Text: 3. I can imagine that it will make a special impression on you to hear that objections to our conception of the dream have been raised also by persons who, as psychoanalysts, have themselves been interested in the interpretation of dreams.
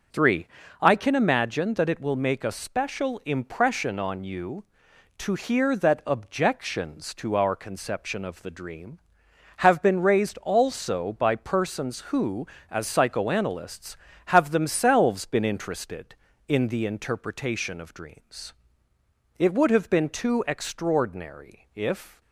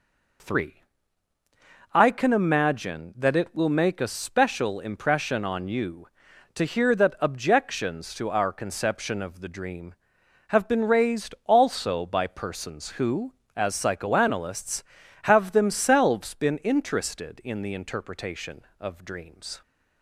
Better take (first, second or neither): second